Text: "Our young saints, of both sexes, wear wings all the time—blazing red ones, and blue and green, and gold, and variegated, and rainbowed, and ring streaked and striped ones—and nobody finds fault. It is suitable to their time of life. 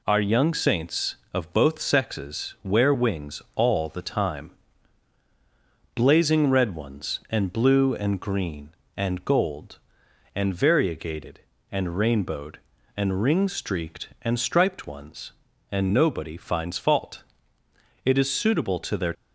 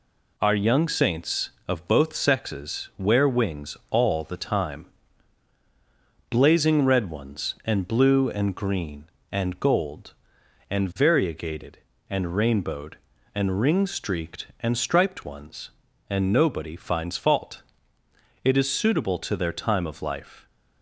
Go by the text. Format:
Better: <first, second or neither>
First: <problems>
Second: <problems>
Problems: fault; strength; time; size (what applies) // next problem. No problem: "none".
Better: second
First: stops before "time of life"; at 19.1 s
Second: none